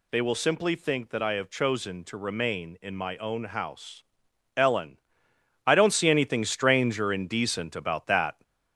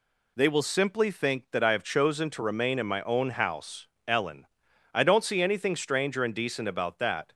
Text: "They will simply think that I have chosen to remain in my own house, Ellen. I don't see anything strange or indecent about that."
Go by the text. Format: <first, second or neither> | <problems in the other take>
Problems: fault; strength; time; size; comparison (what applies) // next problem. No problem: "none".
neither | none